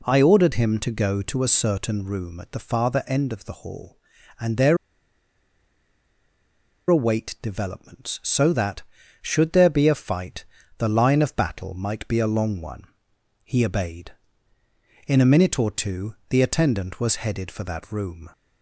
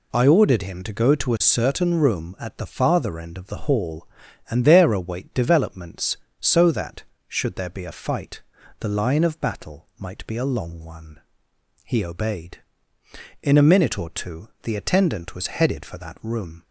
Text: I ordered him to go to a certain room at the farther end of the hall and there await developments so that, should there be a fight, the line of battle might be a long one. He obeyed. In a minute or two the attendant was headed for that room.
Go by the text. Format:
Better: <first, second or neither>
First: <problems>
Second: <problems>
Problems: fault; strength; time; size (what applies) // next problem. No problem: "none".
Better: second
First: pauses between "there" and "await"; strong; at 4.7 s; 2.1 s long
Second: none